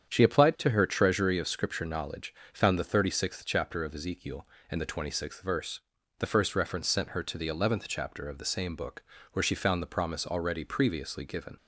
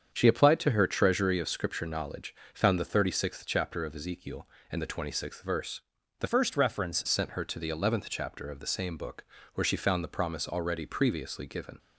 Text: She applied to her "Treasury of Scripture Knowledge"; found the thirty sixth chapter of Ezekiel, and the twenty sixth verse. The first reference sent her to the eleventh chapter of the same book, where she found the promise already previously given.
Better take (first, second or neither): first